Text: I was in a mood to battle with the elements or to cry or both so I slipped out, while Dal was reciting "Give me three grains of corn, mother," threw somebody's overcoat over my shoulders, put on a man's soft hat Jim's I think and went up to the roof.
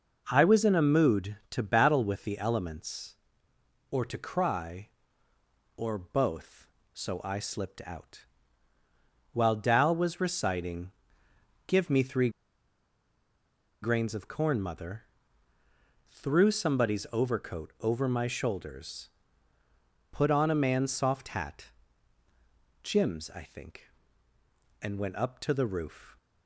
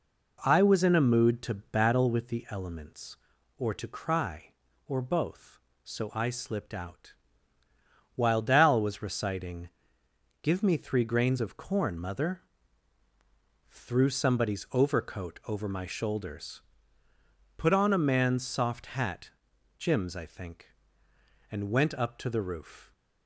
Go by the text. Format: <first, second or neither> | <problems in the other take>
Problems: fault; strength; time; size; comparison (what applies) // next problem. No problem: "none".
second | pauses between "reciting" and "Give"; noticeable; at 10.9 s; 0.74 s long; noticeable in the second // pauses between "three" and "grains"; strong; at 12.3 s; 1.5 s long // pauses between "hat" and "Jim's"; at 21.7 s; 1.1 s long; noticeable in the second